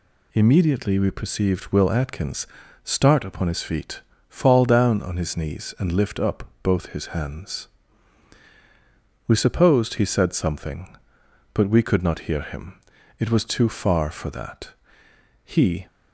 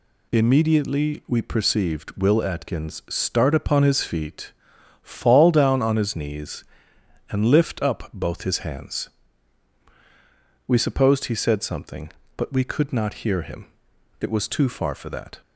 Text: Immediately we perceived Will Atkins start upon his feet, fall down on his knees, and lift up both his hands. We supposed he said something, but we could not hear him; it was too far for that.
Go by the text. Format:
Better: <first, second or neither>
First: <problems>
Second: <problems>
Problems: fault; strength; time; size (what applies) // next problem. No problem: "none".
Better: second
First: pauses between "Atkins" and "start"; at 2.4 s; 0.38 s long // pauses between "up" and "both"; slight; at 6.4 s; 0.18 s long // goes on to say "He"; slight; from 15.4 s on; 0.42 s long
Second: none